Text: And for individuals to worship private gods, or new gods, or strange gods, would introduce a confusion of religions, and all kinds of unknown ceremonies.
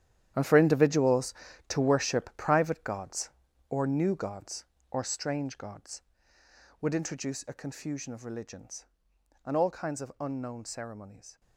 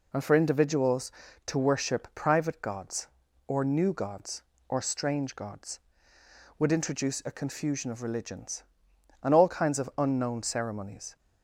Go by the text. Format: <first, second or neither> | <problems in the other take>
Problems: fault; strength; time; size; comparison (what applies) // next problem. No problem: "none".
second | gets quieter; strong; throughout; 13.5 dB